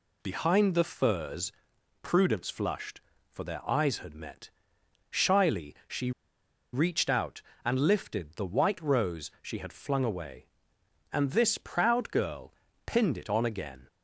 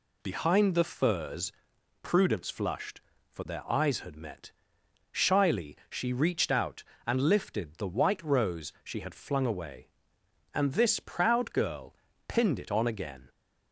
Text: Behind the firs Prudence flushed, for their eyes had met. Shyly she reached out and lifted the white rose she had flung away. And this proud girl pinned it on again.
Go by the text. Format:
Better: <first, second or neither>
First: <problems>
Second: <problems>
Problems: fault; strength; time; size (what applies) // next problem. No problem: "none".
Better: second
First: pauses between "firs" and "Prudence"; noticeable; at 1.5 s; 0.52 s long // pauses between "she" and "reached"; noticeable; at 6.1 s; 0.62 s long // pauses between "girl" and "pinned"; slight; at 12.5 s; 0.34 s long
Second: pauses between "firs" and "Prudence"; noticeable; at 1.5 s; 0.52 s long // pauses between "girl" and "pinned"; slight; at 11.9 s; 0.34 s long